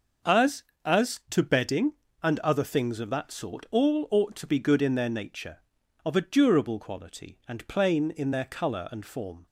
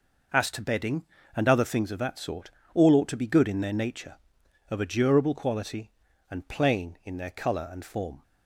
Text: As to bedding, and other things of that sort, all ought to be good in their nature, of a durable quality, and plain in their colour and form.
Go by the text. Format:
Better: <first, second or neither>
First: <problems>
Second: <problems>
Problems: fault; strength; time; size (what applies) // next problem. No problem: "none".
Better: second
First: starts louder than the rest; until 1.5 s; 6.5 dB // says "As" twice; at 0.8 s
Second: none